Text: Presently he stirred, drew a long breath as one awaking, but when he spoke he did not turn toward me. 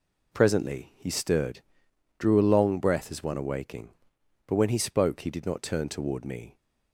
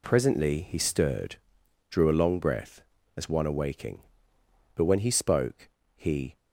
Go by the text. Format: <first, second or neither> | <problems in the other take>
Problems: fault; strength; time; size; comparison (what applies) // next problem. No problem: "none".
first | pauses between "spoke" and "he"; slight; at 5.6 s; 0.26 s long // stops before "did not turn toward me"; at 6.3 s